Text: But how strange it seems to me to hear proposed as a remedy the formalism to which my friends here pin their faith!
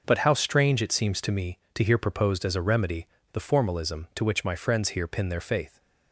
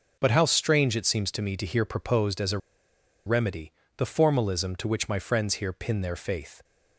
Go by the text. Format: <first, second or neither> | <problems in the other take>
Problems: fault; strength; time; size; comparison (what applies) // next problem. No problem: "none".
first | pauses between "a" and "remedy"; noticeable; at 2.5 s; 0.68 s long // pauses between "remedy" and "the"; slight; at 3.7 s; 0.26 s long; slight in the first